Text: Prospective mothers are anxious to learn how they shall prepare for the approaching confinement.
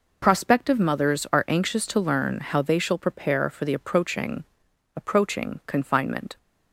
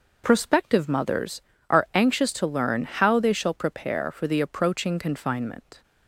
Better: second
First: says "approaching" twice; at 4.9 s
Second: none

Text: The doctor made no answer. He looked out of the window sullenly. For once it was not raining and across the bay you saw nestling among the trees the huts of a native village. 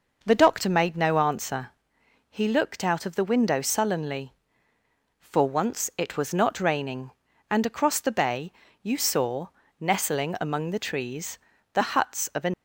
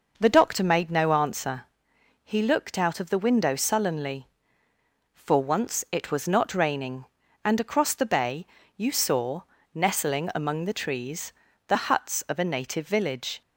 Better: second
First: pauses between "bay" and "you"; slight; at 8.5 s; 0.32 s long // pauses between "saw" and "nestling"; slight; at 9.4 s; 0.32 s long // pauses between "trees" and "the"; slight; at 11.3 s; 0.34 s long // stops before "native village"; at 12.5 s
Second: pauses between "bay" and "you"; slight; at 8.4 s; 0.32 s long // pauses between "saw" and "nestling"; slight; at 9.4 s; 0.32 s long // pauses between "trees" and "the"; slight; at 11.3 s; 0.34 s long

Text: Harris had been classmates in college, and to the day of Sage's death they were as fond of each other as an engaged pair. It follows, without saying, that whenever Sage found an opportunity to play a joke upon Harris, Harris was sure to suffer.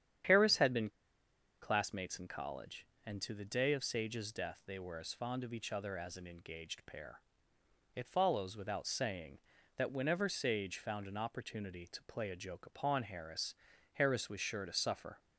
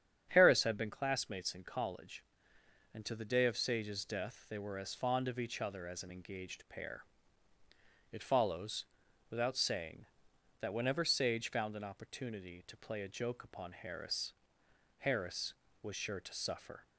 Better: second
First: starts louder than the rest; strong; until 1.9 s; 9.5 dB // pauses between "been" and "classmates"; noticeable; at 0.8 s; 0.72 s long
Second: starts louder than the rest; strong; until 1.3 s; 8.5 dB

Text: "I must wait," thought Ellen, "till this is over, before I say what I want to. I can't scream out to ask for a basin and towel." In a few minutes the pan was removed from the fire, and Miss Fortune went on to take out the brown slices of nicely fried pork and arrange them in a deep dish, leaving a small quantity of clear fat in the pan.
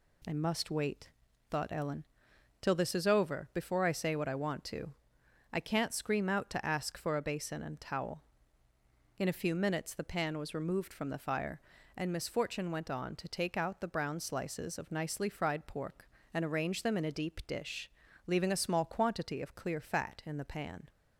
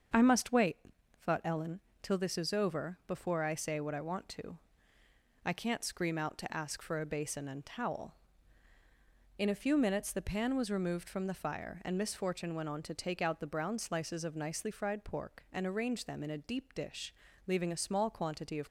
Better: first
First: none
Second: starts louder than the rest; until 1.5 s; 7 dB // stops before "clear fat in the pan"; at 18.6 s

